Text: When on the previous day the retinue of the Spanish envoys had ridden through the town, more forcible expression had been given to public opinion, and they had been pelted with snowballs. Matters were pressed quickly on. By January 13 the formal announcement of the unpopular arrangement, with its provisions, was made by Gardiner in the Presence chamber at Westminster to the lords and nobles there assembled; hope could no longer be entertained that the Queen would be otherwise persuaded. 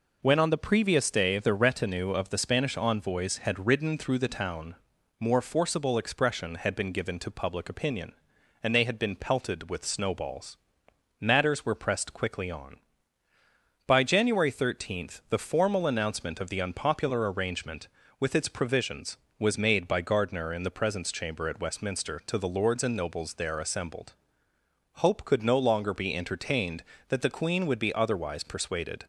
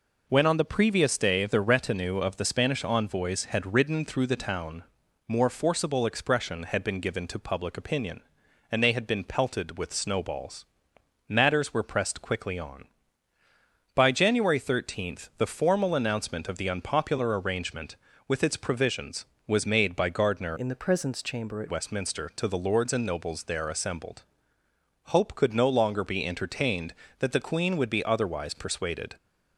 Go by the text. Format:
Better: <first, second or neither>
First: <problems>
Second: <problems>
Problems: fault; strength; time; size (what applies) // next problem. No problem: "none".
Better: first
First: none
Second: changes voice from "in" to "at"; from 20.5 to 21.7 s; 1.2 s long